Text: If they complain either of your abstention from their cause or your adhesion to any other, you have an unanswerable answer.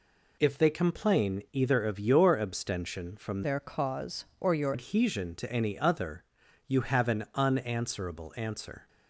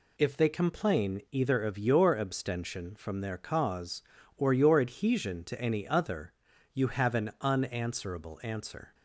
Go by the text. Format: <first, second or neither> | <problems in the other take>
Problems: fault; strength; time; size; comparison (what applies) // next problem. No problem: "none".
second | changes voice from "their" to "your"; from 3.4 to 4.7 s; 1.3 s long